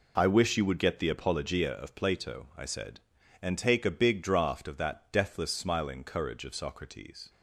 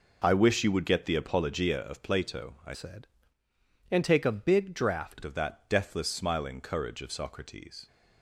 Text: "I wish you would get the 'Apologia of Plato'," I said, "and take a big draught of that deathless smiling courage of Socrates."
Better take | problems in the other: first | changes voice from "said" to "draught"; from 2.7 to 5.2 s; 2.5 s long

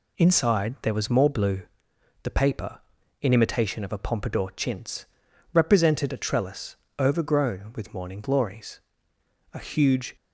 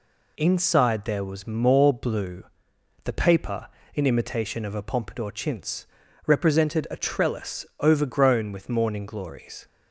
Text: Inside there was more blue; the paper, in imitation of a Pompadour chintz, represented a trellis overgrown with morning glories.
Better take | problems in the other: second | pauses between "trellis" and "overgrown"; slight; at 6.7 s; 0.20 s long; slight in the second // goes on to say "A huge"; noticeable; from 9.5 s on; 0.62 s long

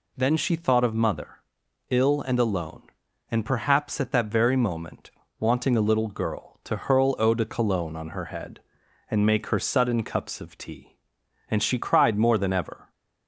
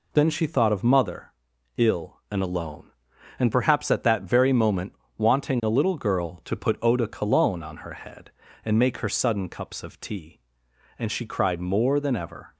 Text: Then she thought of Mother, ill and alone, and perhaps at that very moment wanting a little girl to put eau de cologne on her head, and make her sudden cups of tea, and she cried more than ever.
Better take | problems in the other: second | pauses between "moment" and "wanting"; slight; at 5.0 s; 0.30 s long; slight in the second // says "hurl" for "put"; at 6.7 s

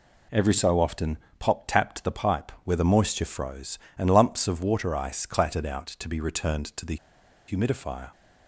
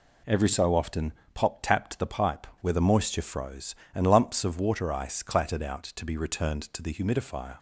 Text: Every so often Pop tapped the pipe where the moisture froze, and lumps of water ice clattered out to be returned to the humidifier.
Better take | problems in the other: second | pauses between "often" and "Pop"; slight; at 1.1 s; 0.22 s long; slight in the second // pauses between "the" and "humidifier"; noticeable; at 6.9 s; 0.52 s long

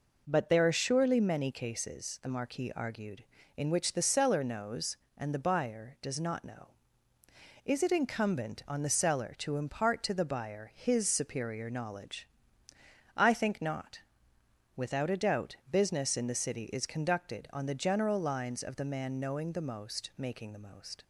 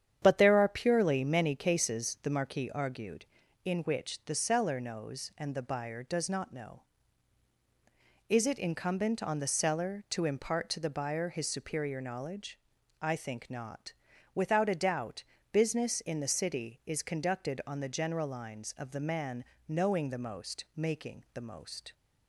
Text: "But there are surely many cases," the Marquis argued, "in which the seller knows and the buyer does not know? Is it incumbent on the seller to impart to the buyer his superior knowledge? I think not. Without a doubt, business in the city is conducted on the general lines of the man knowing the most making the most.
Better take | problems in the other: first | starts louder than the rest; strong; until 1.2 s; 9 dB // says "purely" for "surely"; at 0.6 s // pauses between "man" and "knowing"; slight; at 19.4 s; 0.24 s long

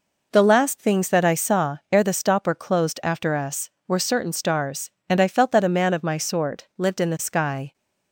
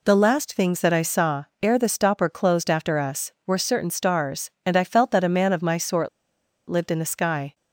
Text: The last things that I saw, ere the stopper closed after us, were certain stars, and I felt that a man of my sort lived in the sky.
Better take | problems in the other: first | pauses between "sort" and "lived"; noticeable; at 6.0 s; 0.59 s long

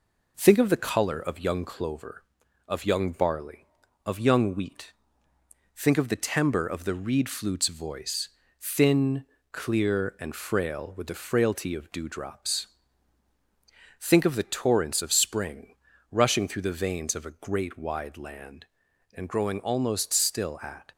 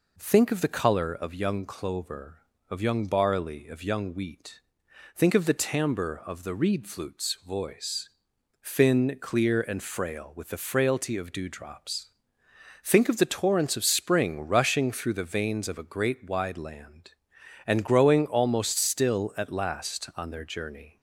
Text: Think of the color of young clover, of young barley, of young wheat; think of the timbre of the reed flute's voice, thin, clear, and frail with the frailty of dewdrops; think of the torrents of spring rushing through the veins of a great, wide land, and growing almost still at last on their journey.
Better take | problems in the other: second | pauses between "spring" and "rushing"; at 15.7 s; 0.38 s long // stops before "last on their journey"; at 20.9 s

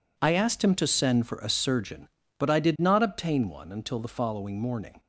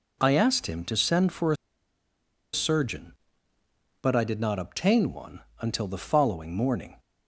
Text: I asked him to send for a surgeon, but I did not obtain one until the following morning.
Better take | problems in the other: first | pauses between "a" and "surgeon"; noticeable; at 1.5 s; 0.97 s long // pauses between "one" and "until"; slight; at 5.3 s; 0.20 s long

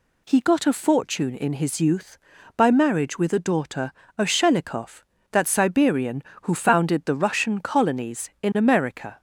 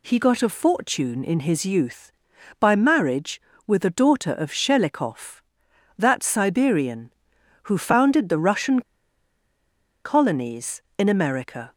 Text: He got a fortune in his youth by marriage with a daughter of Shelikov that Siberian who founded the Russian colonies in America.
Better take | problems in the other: first | pauses between "Russian" and "colonies"; at 8.8 s; 1.2 s long

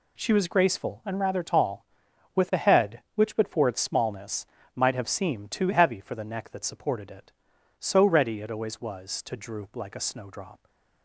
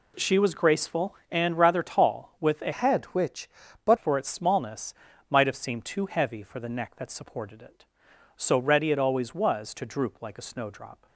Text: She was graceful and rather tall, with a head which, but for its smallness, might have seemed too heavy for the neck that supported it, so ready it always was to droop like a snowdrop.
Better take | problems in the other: first | changes voice from "head" to "but"; from 2.7 to 3.9 s; 1.2 s long

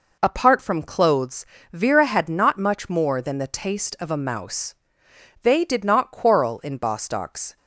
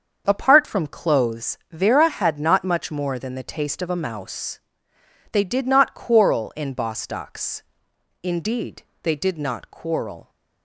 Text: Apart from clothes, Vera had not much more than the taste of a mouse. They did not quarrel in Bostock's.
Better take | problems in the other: first | starts louder than the rest; until 1.2 s; 7 dB // goes on to say "Indeed they did not quarrel"; strong; from 8.2 s on; 2.0 s long

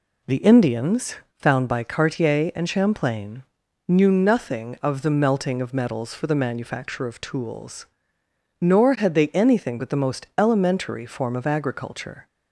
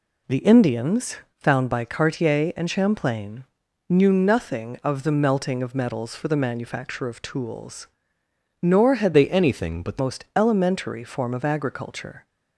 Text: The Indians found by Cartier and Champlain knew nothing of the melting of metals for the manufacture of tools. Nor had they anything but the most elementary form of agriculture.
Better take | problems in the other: first | pauses between "Indians" and "found"; slight; at 1.1 s; 0.20 s long; slight in the first // pauses between "Champlain" and "knew"; noticeable; at 3.4 s; 0.46 s long; noticeable in the first // changes voice from "they" to "the"; from 9.1 to 9.9 s; 0.8 s long

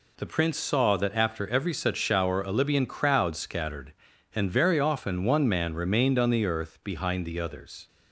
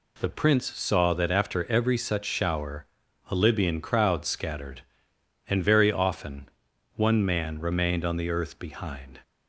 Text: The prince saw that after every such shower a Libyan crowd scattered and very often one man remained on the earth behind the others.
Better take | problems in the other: first | pauses between "shower" and "a"; at 2.8 s; 0.42 s long // pauses between "often" and "one"; noticeable; at 6.4 s; 0.46 s long // stops before "the others"; at 9.2 s

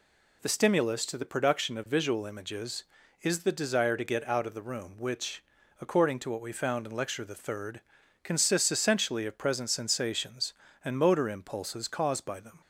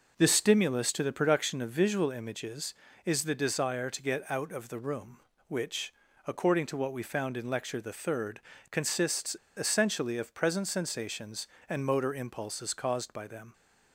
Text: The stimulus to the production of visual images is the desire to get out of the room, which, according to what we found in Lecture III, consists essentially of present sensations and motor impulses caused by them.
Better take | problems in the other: first | pauses between "consists" and "essentially"; slight; at 9.3 s; 0.23 s long

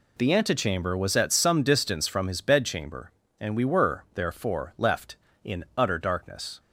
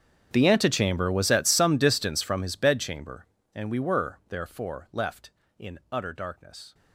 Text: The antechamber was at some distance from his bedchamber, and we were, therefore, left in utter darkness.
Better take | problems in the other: first | gets quieter; strong; throughout; 23 dB

